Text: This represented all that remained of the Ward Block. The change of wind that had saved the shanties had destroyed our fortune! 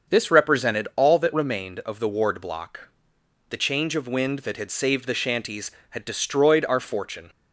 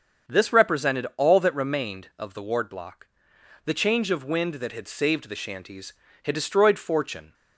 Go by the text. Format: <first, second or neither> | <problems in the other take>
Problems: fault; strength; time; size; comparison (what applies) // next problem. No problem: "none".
first | starts louder than the rest; until 1.3 s; 7 dB; also in the first // skips "our"; at 6.7 s